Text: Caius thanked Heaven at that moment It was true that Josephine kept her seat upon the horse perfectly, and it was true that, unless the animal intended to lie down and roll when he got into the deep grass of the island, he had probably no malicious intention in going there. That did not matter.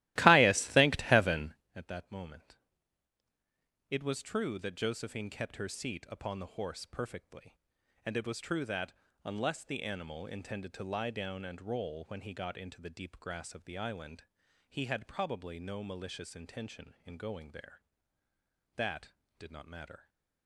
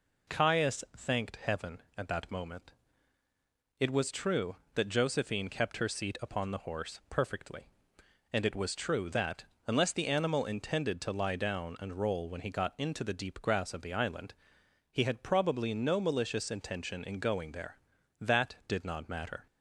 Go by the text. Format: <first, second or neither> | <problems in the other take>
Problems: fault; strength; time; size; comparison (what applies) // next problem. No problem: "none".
second | starts louder than the rest; strong; until 1.7 s; 16.5 dB // pauses between "moment" and "It"; strong; at 2.5 s; 1.3 s long; also in the second